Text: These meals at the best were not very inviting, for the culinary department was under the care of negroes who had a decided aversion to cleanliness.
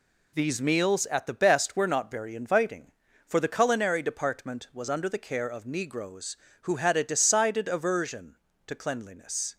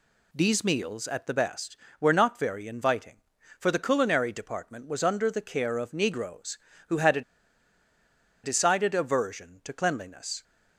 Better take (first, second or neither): first